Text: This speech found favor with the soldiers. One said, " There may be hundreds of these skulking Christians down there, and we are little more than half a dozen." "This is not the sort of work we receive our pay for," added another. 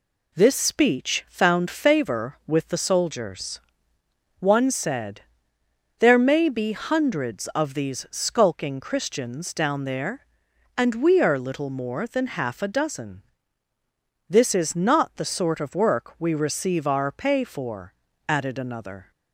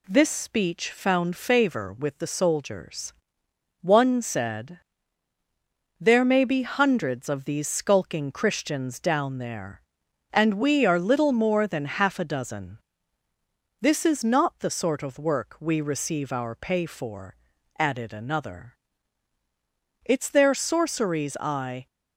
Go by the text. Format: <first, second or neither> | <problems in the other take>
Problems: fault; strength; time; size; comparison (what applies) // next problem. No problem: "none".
first | goes on to say "It's their sorceries I"; strong; from 20.0 s on; 1.8 s long